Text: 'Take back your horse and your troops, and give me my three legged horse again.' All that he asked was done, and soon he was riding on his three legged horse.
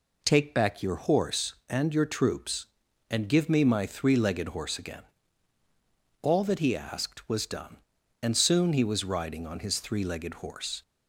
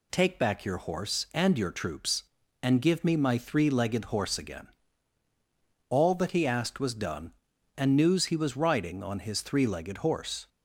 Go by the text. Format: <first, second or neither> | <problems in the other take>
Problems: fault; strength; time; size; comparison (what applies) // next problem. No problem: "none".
first | says "news" for "soon"; at 7.9 s